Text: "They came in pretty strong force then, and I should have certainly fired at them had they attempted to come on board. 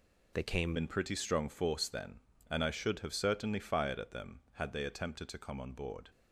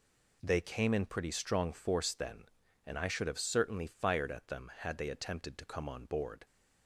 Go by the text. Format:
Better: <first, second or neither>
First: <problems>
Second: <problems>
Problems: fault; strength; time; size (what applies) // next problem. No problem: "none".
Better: second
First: changes voice at "in"; from 0.7 s on; 5.3 s long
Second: none